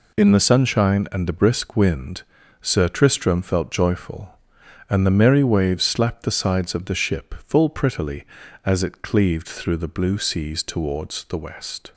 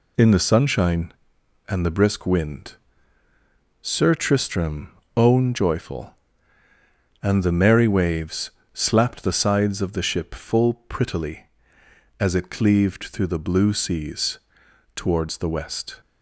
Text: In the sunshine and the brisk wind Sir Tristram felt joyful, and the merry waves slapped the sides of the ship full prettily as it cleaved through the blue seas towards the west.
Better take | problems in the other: first | pauses between "wind" and "Sir"; at 2.7 s; 1.0 s long; also in the first // says "own" for "felt"; at 5.1 s // pauses between "waves" and "slapped"; slight; at 8.5 s; 0.22 s long // pauses between "seas" and "towards"; noticeable; at 14.3 s; 0.56 s long

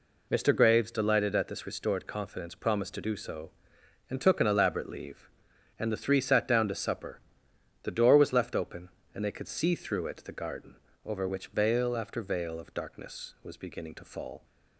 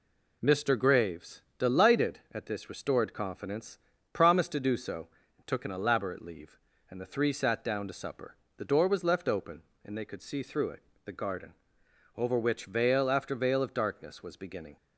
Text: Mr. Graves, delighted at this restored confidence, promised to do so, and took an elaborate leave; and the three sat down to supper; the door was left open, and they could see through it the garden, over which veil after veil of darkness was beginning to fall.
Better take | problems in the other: first | pauses between "it" and "the"; slight; at 10.8 s; 0.22 s long // stops before "to fall"; at 14.7 s

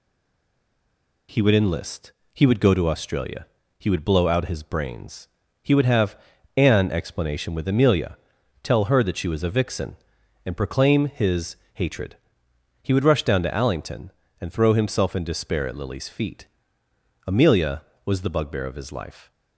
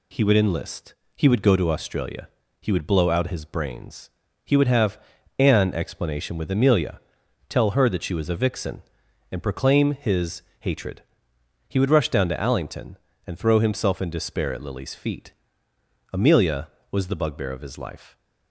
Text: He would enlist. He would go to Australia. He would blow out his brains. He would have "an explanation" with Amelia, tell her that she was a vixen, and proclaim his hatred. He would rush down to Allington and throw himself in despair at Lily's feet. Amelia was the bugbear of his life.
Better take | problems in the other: second | stays silent before the first word; noticeable; until 1.2 s; 1.2 s long // pauses between "have" and "an"; at 6.1 s; 0.38 s long; also in the second // pauses between "his" and "hatred"; slight; at 11.5 s; 0.20 s long; slight in the second

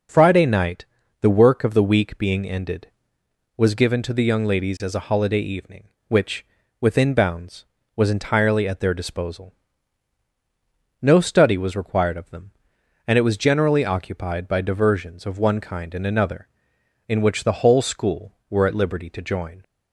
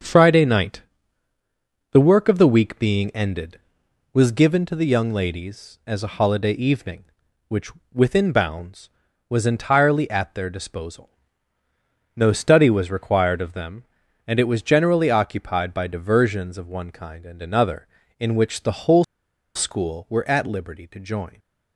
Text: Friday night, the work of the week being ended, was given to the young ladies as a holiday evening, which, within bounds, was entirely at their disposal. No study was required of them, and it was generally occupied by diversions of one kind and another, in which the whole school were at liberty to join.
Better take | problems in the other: first | starts louder than the rest; until 2.1 s; 6.5 dB // pauses between "whole" and "school"; noticeable; at 19.0 s; 0.51 s long

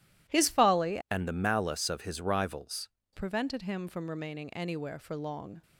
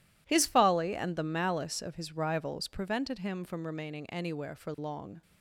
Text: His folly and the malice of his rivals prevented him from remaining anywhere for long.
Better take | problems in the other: second | changes voice from "and" to "rivals"; from 1.1 to 2.8 s; 1.7 s long

